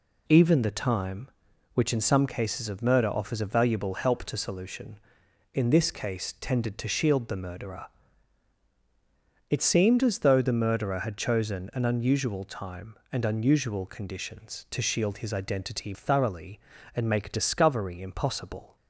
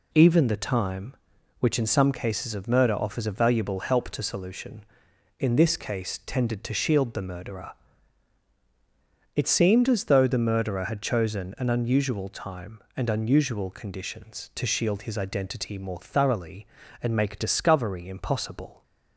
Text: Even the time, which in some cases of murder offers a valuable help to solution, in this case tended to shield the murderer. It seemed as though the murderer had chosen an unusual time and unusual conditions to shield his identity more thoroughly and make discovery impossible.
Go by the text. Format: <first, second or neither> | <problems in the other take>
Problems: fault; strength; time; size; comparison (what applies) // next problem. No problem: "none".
second | skips "more"; at 15.9 s